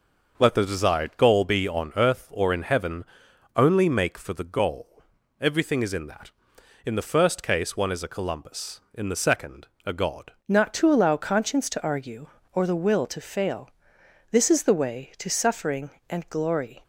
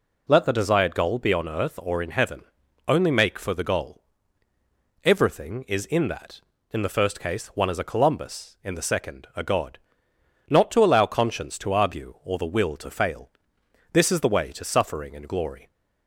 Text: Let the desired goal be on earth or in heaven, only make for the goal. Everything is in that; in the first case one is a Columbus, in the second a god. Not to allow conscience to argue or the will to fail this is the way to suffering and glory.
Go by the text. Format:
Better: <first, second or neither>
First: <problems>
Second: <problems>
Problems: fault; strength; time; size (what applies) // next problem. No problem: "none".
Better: second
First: starts louder than the rest; noticeable; until 1.3 s; 6 dB // pauses between "second" and "a"; slight; at 9.6 s; 0.18 s long // changes voice at "Not"; from 10.4 s on; 6.4 s long // pauses between "fail" and "this"; noticeable; at 13.6 s; 0.62 s long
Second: pauses between "fail" and "this"; noticeable; at 13.2 s; 0.62 s long